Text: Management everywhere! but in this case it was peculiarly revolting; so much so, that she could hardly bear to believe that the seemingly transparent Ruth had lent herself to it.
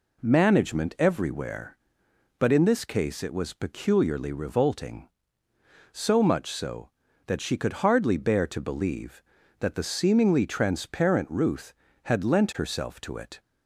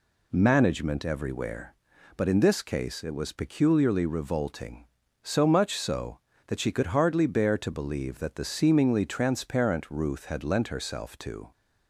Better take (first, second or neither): first